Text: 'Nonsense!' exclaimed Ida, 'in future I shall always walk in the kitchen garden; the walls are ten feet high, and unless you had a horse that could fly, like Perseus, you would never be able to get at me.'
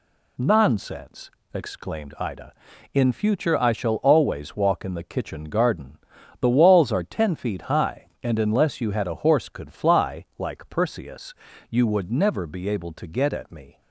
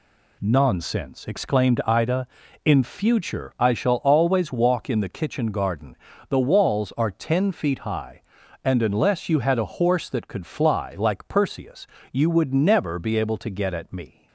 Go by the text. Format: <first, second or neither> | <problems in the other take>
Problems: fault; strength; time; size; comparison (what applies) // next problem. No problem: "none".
second | skips "that"; at 9.4 s